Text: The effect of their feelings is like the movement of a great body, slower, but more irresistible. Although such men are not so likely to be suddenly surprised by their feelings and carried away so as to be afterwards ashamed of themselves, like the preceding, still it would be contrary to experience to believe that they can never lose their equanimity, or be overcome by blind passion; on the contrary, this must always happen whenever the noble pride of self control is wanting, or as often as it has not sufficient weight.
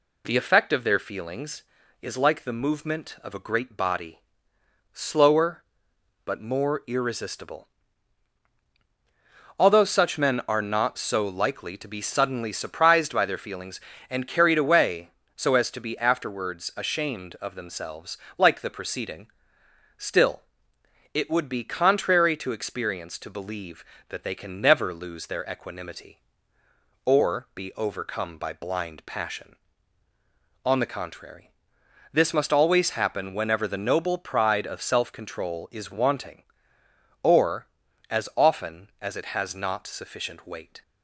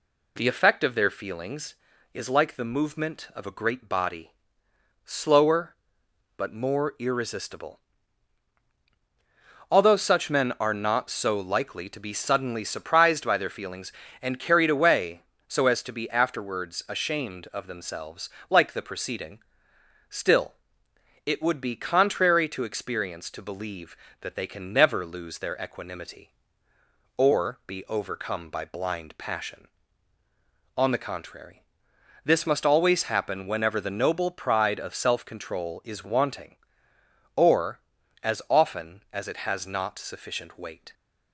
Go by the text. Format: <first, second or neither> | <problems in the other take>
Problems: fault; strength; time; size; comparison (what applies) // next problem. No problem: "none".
neither | pauses between "still" and "it"; noticeable; the same in both